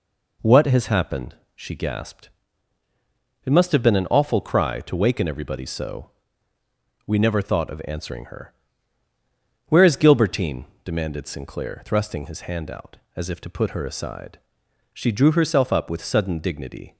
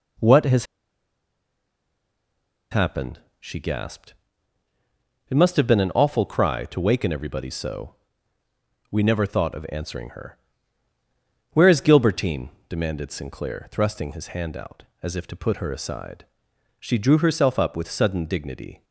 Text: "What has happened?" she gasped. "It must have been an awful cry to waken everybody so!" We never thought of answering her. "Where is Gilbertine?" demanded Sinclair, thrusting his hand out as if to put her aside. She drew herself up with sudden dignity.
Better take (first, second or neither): first